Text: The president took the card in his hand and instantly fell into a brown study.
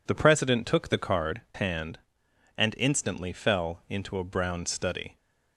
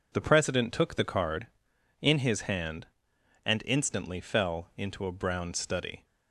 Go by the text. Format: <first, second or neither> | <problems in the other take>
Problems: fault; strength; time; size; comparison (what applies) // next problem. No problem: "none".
second | skips "in his"; at 1.4 s